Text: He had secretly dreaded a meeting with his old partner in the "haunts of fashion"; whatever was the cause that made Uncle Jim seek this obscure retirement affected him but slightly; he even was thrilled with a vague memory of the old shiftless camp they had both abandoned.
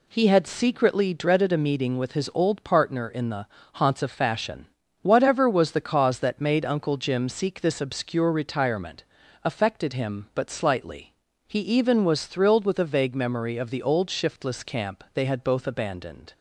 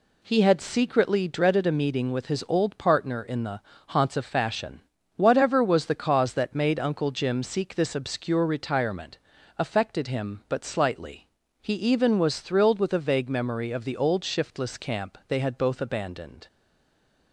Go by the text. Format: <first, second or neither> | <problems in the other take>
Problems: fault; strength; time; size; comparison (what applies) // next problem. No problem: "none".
first | pauses between "the" and "haunts"; slight; at 3.5 s; 0.28 s long; slight in the first // pauses between "retirement" and "affected"; at 9.1 s; 0.40 s long; also in the first // stays silent after the last word; slight; from 16.4 s on; 0.9 s long